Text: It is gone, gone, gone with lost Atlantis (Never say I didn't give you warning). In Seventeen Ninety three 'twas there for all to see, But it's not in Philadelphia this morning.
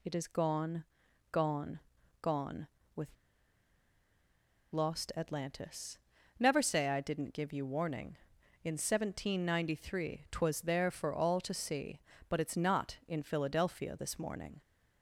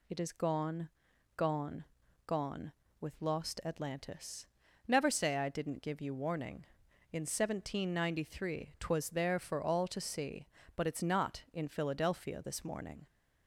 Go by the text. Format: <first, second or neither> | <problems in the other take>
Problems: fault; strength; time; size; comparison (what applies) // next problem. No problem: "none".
second | pauses between "with" and "lost"; strong; at 3.0 s; 1.6 s long